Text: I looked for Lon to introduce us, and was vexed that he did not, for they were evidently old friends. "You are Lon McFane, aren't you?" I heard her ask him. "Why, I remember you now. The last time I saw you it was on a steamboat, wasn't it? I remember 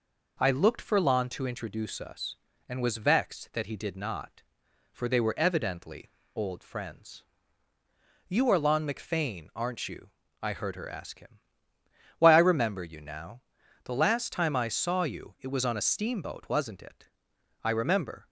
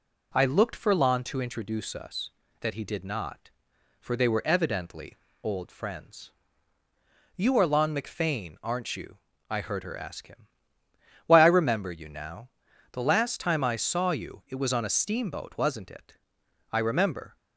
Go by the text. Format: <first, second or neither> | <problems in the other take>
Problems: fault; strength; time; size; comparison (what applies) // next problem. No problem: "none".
first | skips "and was vexed"; at 2.4 s // pauses between "evidently" and "old"; slight; at 5.1 s; 0.28 s long; slight in the first